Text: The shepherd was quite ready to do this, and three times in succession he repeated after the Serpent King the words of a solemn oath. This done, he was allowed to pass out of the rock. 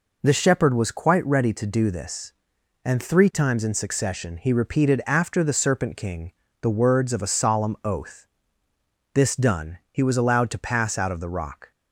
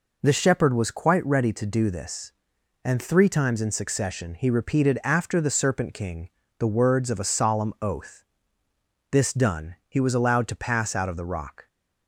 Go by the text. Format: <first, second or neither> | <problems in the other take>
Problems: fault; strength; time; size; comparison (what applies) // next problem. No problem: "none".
neither | pauses between "King" and "the"; slight; the same in both